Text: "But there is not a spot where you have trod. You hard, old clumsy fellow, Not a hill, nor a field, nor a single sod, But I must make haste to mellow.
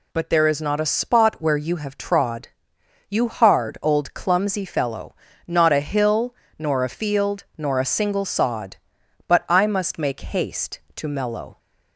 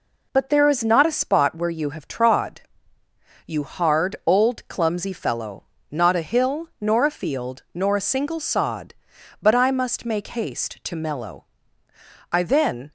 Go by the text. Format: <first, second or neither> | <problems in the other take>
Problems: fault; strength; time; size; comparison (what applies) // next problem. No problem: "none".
first | goes on to say "I then"; from 12.3 s on; 0.60 s long